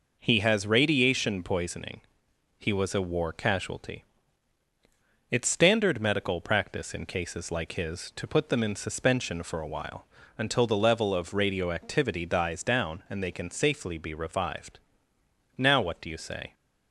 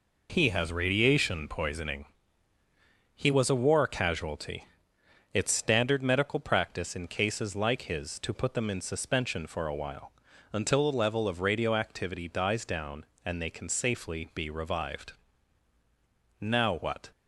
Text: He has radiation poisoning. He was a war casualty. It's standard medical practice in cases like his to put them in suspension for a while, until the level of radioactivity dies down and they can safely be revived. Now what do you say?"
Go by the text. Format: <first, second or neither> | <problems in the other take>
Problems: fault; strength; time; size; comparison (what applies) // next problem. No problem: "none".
first | stops before "do you say"; at 17.1 s